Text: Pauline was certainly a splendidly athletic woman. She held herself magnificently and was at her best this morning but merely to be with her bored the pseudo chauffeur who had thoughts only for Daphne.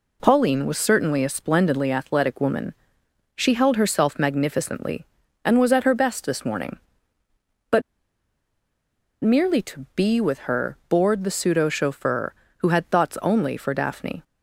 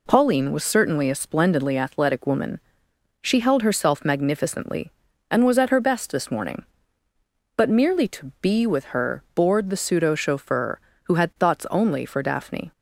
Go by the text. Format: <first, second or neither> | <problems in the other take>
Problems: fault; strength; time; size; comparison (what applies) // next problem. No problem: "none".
second | pauses between "but" and "merely"; strong; at 7.8 s; 1.4 s long